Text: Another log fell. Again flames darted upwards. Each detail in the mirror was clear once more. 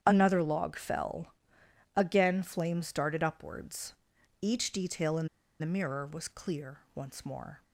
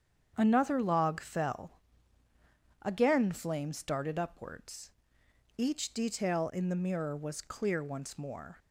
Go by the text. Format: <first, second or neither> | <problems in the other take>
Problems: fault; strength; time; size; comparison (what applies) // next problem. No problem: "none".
second | starts louder than the rest; strong; until 1.0 s; 9 dB; strong in the second // pauses between "in" and "the"; slight; at 5.2 s; 0.32 s long // pauses between "clear" and "once"; slight; at 6.7 s; 0.16 s long